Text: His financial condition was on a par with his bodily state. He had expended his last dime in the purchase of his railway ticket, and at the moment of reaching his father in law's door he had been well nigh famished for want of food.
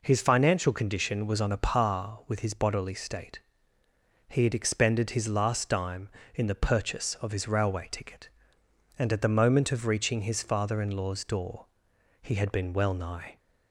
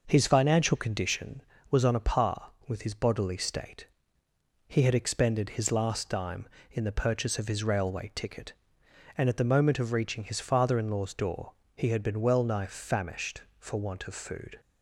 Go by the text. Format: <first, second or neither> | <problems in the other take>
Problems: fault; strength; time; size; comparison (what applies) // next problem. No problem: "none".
second | pauses between "door" and "he"; noticeable; at 11.6 s; 0.54 s long; slight in the second // stops before "famished for want of food"; at 13.3 s